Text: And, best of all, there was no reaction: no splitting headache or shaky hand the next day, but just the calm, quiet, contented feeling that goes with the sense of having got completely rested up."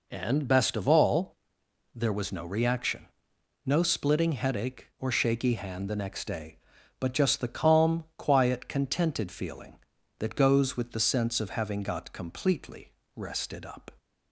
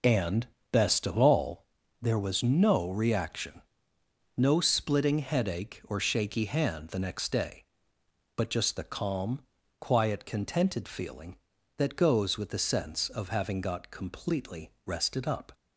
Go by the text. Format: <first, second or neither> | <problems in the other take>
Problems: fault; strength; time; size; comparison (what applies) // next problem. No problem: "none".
first | loses the start of "And"; at 0.0 s; 20 ms // pauses between "completely" and "rested"; slight; at 14.7 s; 0.16 s long; slight in the first